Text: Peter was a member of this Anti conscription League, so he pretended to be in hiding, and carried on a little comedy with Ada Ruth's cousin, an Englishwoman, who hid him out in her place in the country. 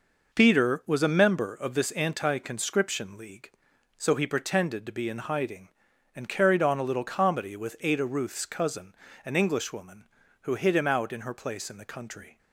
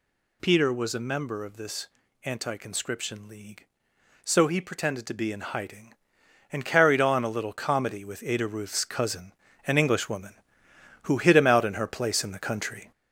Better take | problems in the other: first | gets louder; noticeable; throughout; 4.5 dB // pauses between "this" and "Anti"; slight; at 1.8 s; 0.36 s long

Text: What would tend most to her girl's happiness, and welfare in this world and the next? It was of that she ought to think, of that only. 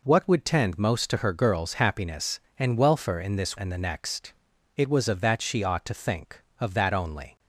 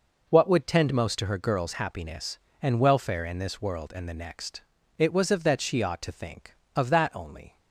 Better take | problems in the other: second | skips "world"; at 3.5 s

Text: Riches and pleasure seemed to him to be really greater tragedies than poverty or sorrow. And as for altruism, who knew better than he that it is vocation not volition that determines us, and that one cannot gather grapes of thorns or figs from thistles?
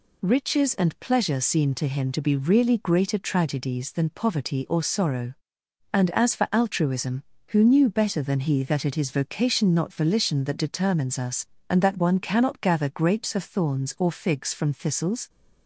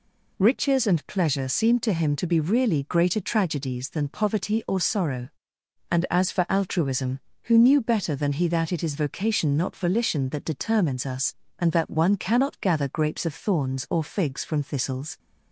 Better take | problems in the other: neither | none

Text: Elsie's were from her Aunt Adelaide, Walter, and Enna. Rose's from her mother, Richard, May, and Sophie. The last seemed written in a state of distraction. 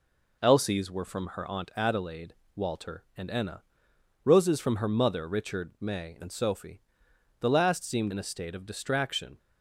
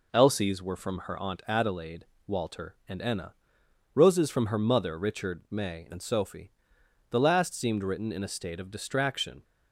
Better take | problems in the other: second | skips "written"; at 8.1 s

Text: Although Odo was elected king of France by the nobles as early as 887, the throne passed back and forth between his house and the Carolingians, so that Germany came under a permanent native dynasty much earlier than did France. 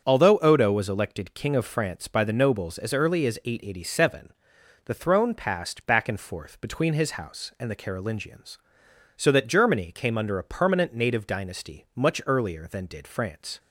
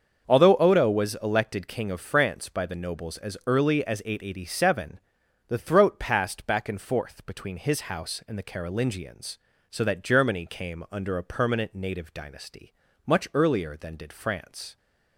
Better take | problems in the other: first | starts louder than the rest; until 1.3 s; 6.5 dB; also in the first // says "throat" for "throne"; at 5.5 s // pauses between "dynasty" and "much"; slight; at 12.7 s; 0.34 s long

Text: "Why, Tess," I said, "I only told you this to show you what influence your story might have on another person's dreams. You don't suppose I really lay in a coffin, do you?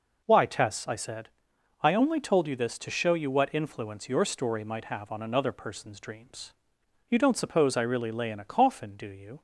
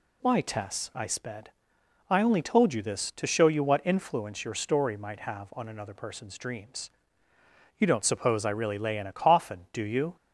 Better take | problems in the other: first | says "sped" for "said"; at 1.0 s

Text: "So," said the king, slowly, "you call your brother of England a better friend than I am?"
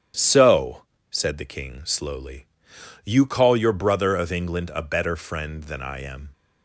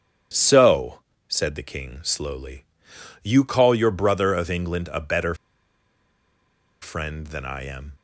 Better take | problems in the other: first | starts louder than the rest; strong; until 1.6 s; 8.5 dB; strong in the first // pauses between "better" and "friend"; strong; at 5.3 s; 1.4 s long

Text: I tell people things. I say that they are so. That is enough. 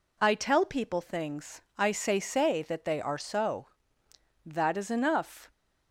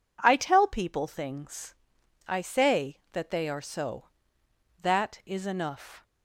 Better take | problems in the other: second | says "say" twice; at 2.1 s

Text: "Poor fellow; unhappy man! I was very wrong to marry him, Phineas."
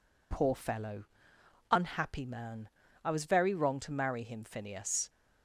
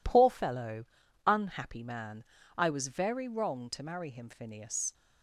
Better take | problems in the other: neither | none

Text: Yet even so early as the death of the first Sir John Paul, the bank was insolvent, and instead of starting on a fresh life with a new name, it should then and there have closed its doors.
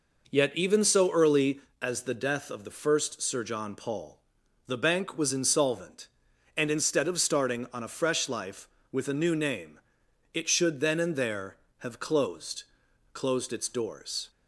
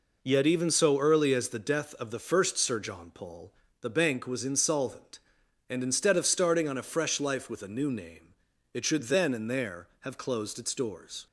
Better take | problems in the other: second | says "closed" twice; at 13.1 s

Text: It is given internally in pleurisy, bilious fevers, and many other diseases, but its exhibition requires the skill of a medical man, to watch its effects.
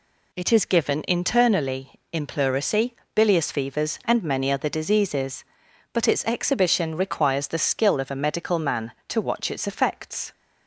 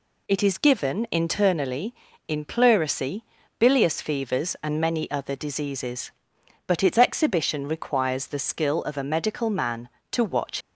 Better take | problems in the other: first | stops before "its effects"; at 10.6 s

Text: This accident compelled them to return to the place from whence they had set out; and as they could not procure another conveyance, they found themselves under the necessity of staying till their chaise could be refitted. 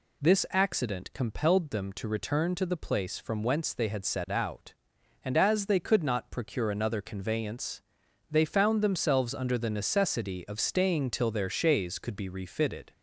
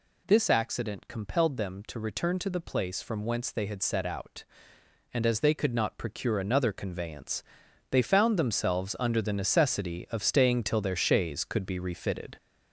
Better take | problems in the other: first | gets louder; noticeable; throughout; 4.5 dB

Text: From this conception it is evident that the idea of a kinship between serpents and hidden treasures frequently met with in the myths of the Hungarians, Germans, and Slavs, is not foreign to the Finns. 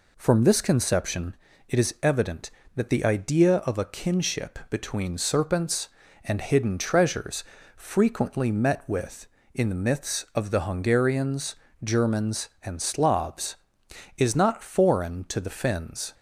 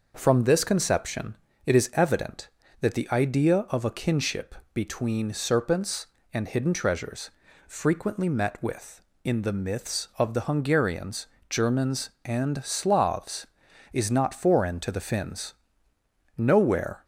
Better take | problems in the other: first | starts louder than the rest; noticeable; until 1.1 s; 6 dB // pauses between "conception" and "it"; slight; at 1.3 s; 0.32 s long; slight in the first // pauses between "kinship" and "between"; slight; at 4.5 s; 0.18 s long // pauses between "treasures" and "frequently"; slight; at 7.2 s; 0.36 s long; slight in the first // goes on to say "Nowhere"; noticeable; from 16.3 s on; 0.66 s long

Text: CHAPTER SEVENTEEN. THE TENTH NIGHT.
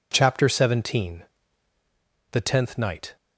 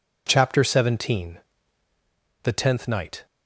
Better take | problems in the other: neither | none

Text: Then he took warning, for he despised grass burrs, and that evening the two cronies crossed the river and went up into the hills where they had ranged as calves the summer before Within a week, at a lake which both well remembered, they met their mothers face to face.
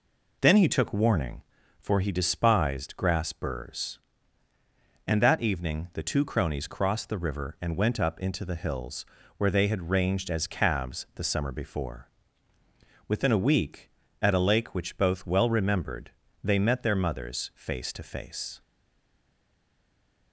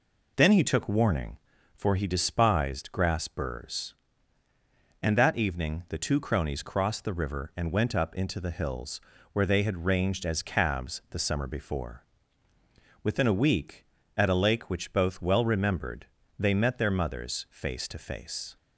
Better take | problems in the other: second | pauses between "hills" and "where"; slight; at 9.0 s; 0.32 s long; slight in the second // pauses between "before" and "Within"; at 12.0 s; 1.0 s long; also in the second // stays silent after the last word; noticeable; from 18.6 s on; 1.7 s long

